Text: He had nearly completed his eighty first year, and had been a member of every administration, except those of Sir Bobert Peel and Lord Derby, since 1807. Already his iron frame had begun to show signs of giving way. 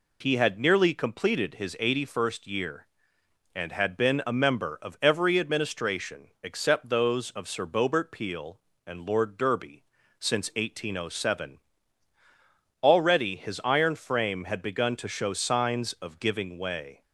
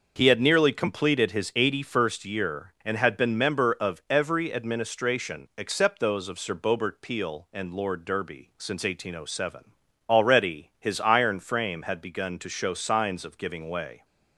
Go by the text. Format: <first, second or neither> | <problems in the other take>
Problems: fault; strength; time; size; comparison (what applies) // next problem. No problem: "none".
first | skips "a"; at 3.3 s